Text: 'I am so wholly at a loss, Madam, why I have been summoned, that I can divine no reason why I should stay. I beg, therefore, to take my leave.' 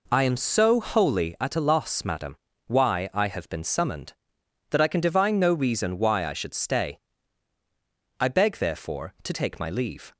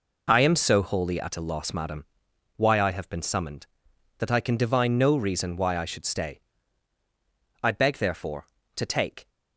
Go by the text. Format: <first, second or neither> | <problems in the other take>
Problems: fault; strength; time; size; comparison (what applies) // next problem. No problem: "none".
first | stops before "my leave"; at 9.2 s